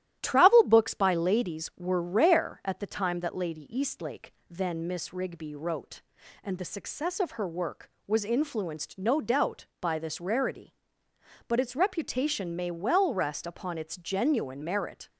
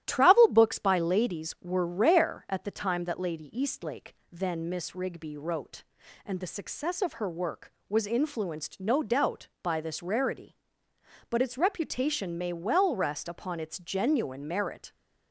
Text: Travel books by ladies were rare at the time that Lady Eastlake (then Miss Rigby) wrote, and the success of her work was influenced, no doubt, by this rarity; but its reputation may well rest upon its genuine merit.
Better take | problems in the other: neither | starts louder than the rest; strong; the same in both

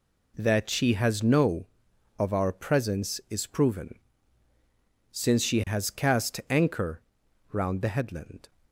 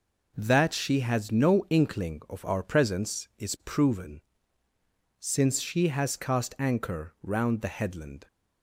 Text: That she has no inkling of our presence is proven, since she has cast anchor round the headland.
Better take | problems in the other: second | skips "inkling"; at 1.9 s // pauses between "anchor" and "round"; noticeable; at 7.0 s; 0.48 s long

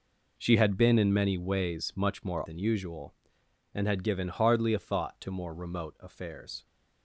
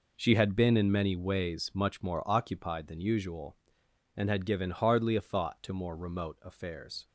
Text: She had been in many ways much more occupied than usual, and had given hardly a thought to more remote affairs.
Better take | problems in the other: second | skips "occupied"; at 2.4 s

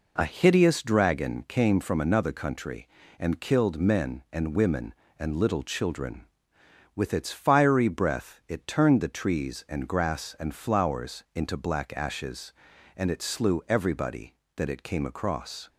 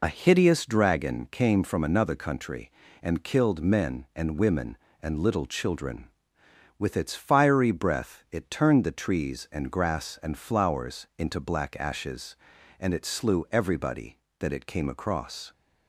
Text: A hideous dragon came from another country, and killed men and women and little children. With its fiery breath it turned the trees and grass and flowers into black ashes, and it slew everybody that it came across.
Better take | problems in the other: first | loses the start of "A"; at 0.0 s; 35 ms

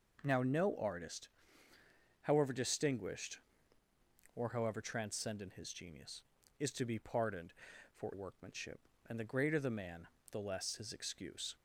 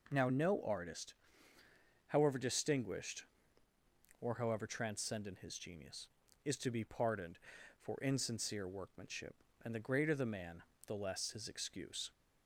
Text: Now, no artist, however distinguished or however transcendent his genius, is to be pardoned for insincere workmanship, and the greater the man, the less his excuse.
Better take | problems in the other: second | skips "insincere"; at 8.1 s

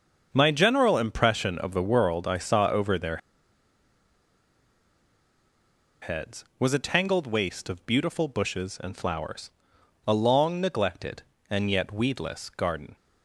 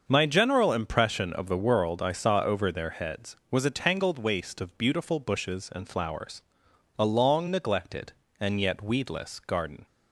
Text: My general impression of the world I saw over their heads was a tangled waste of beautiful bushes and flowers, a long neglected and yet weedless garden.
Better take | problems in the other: second | starts louder than the rest; until 1.3 s; 6.5 dB; also in the second // pauses between "their" and "heads"; strong; at 3.1 s; 2.8 s long

